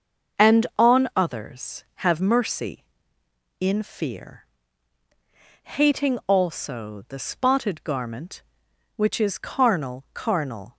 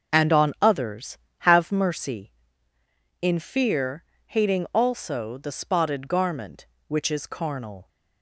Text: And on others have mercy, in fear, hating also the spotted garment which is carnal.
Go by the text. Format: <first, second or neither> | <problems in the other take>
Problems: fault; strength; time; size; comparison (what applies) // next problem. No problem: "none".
second | starts louder than the rest; until 1.5 s; 6.5 dB; also in the second // says "carnal" twice; at 10.1 s